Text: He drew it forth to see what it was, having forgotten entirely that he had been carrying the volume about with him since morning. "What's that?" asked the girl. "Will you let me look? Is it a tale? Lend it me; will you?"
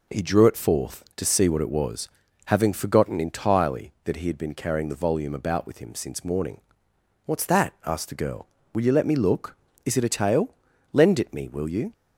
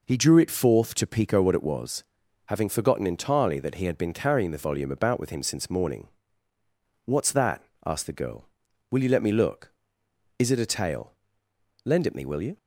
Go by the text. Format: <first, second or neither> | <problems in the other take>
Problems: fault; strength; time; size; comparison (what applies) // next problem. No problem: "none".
first | says "pico" for "see"; at 1.0 s